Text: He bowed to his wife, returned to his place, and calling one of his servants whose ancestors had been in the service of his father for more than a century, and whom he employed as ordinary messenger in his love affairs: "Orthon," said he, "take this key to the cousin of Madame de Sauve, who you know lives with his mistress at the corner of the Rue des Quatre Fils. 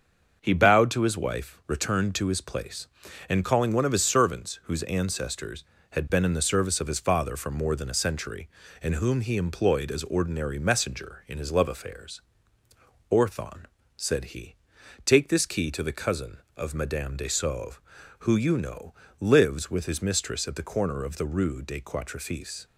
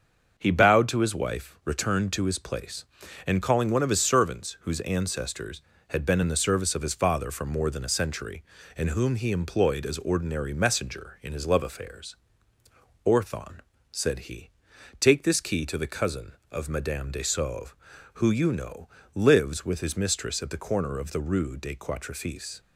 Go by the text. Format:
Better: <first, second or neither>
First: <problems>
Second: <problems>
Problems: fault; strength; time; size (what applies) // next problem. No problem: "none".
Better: neither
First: starts louder than the rest; until 1.4 s; 7 dB // pauses between "know" and "lives"; slight; at 18.9 s; 0.24 s long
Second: starts louder than the rest; until 1.4 s; 7 dB // pauses between "know" and "lives"; slight; at 18.8 s; 0.24 s long